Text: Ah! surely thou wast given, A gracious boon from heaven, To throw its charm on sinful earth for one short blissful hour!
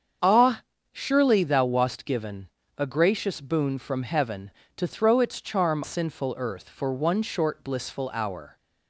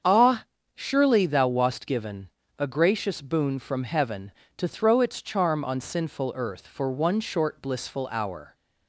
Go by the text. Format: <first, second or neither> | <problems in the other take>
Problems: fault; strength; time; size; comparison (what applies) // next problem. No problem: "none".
second | starts louder than the rest; strong; until 1.5 s; 7 dB; strong in the second // skips "on"; at 5.8 s